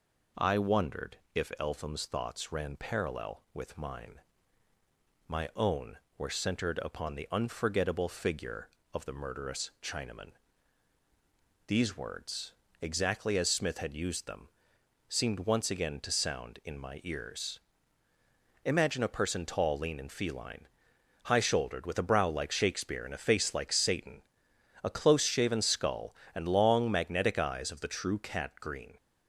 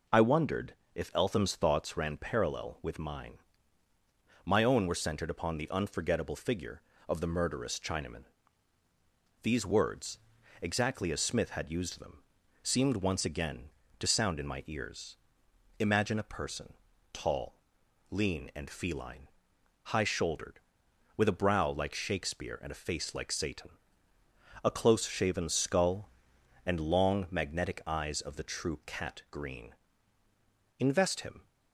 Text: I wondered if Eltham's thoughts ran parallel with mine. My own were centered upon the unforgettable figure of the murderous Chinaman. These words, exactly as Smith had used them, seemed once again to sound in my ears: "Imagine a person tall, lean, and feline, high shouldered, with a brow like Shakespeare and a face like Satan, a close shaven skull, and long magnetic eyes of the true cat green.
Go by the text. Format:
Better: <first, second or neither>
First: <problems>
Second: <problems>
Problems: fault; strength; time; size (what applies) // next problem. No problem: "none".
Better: first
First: pauses between "wondered" and "if"; slight; at 1.1 s; 0.18 s long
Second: pauses between "wondered" and "if"; slight; at 0.7 s; 0.22 s long // pauses between "person" and "tall"; at 16.7 s; 0.38 s long // goes on to say "Invest him"; noticeable; from 30.7 s on; 0.68 s long